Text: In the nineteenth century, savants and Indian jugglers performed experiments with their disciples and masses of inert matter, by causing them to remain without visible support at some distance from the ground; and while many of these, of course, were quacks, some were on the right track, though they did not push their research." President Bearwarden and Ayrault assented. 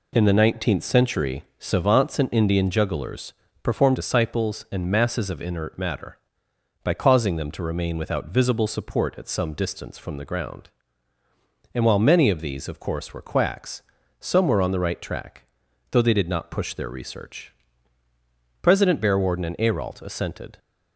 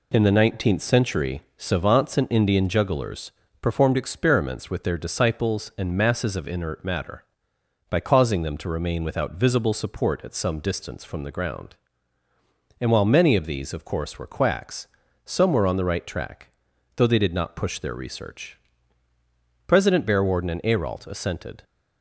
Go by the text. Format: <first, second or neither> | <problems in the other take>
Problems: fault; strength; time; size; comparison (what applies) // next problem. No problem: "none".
second | pauses between "jugglers" and "performed"; slight; at 3.3 s; 0.32 s long; slight in the second // skips "experiments with their"; at 3.9 s